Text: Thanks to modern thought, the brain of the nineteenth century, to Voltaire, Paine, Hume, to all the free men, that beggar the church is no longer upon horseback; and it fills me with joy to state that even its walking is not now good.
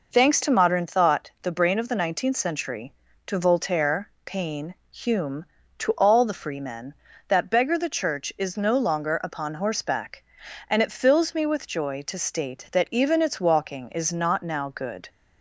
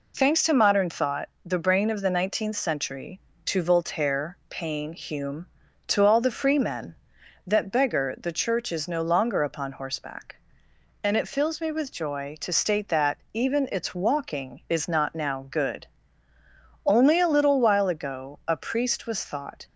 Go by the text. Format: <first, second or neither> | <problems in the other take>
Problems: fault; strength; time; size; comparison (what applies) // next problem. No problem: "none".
first | pauses between "that" and "even"; slight; at 13.1 s; 0.16 s long // goes on to say "Only a little while ago a priest was thought"; strong; from 16.8 s on; 2.8 s long